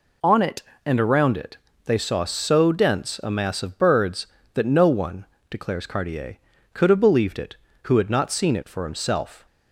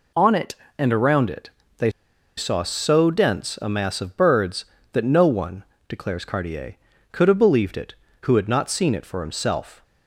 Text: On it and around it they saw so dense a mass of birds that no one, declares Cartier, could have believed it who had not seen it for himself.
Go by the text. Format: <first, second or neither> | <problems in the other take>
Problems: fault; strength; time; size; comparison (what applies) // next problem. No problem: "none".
first | pauses between "it" and "they"; slight; at 1.4 s; 0.30 s long; slight in the first // pauses between "they" and "saw"; noticeable; at 1.8 s; 0.48 s long